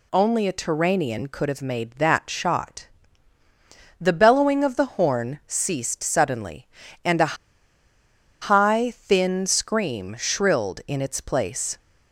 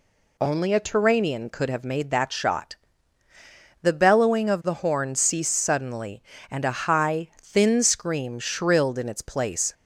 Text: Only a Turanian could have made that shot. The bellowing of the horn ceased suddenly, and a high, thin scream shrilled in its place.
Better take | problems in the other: second | pauses between "a" and "high"; at 7.3 s; 1.0 s long

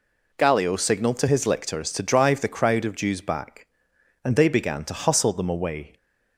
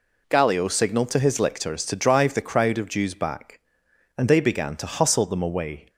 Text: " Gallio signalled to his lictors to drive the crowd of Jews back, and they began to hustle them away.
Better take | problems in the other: neither | none

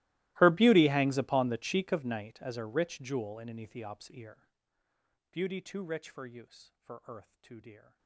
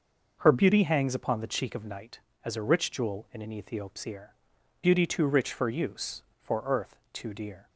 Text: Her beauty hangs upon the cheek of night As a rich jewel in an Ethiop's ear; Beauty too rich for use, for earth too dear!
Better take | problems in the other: second | gets quieter; strong; throughout; 28 dB

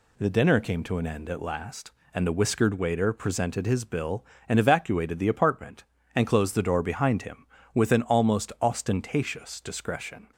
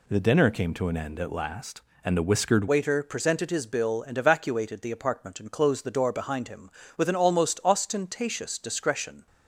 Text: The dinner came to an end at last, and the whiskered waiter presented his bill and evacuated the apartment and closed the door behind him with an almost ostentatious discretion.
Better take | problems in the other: first | changes voice at "waiter"; from 2.6 s on; 6.6 s long

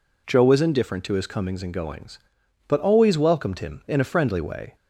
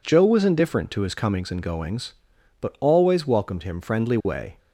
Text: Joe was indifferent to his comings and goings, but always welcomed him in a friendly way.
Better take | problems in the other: first | skips "in a"; at 3.7 s

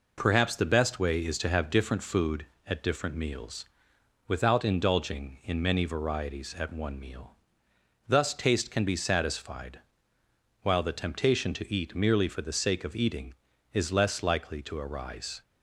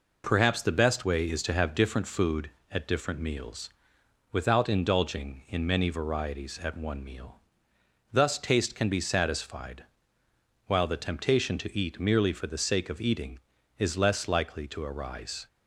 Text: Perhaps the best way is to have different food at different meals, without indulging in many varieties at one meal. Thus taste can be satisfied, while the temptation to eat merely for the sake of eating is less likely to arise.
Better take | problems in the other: neither | none

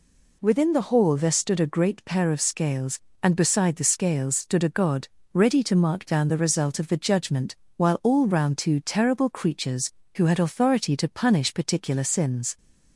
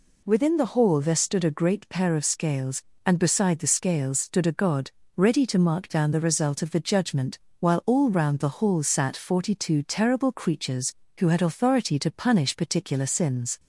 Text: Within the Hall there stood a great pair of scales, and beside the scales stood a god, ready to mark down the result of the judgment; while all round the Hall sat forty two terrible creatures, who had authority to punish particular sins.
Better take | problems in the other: second | skips "the Hall sat forty"; at 8.5 s

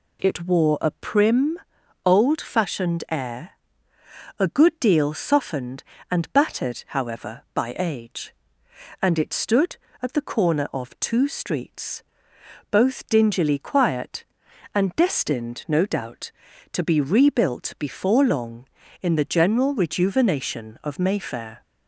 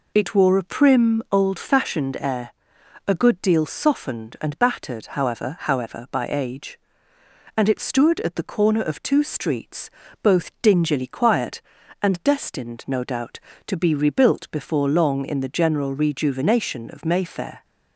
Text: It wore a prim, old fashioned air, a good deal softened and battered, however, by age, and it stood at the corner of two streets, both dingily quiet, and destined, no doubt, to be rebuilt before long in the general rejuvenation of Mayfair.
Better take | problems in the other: first | says "however" twice; at 5.6 s

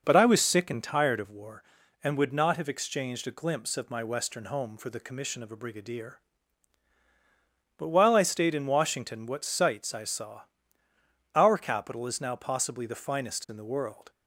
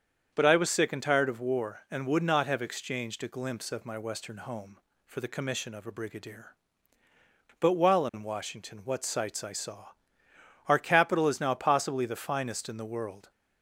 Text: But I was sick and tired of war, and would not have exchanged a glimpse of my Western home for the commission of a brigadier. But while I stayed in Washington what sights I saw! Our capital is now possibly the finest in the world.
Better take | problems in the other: first | starts louder than the rest; strong; until 1.3 s; 7 dB // skips "I stayed"; at 8.0 s

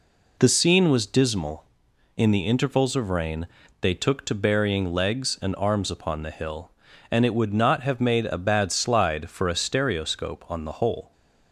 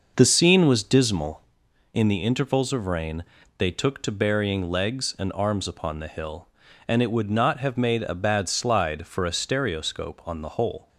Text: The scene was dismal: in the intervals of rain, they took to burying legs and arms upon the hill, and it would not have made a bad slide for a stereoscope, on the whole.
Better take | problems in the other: first | starts louder than the rest; noticeable; until 1.6 s; 6 dB

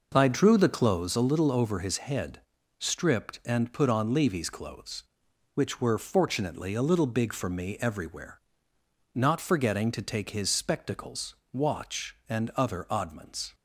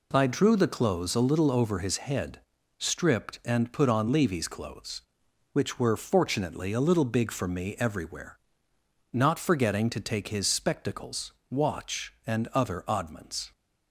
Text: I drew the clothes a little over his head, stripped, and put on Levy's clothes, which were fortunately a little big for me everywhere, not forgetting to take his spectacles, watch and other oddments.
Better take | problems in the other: second | starts louder than the rest; noticeable; until 1.1 s; 5.5 dB

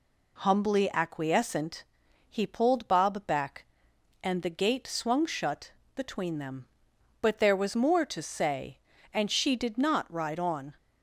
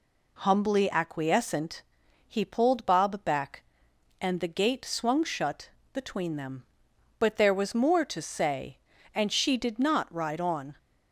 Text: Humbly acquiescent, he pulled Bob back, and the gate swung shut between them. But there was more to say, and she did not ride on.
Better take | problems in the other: neither | pauses between "shut" and "between"; slight; the same in both

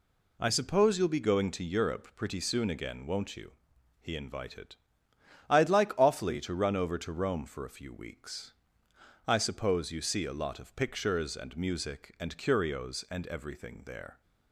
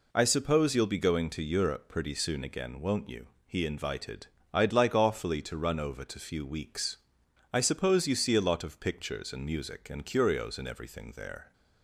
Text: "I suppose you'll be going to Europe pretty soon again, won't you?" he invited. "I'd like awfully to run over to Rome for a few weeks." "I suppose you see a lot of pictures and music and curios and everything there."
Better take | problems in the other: first | skips "Rome for a"; at 6.1 s

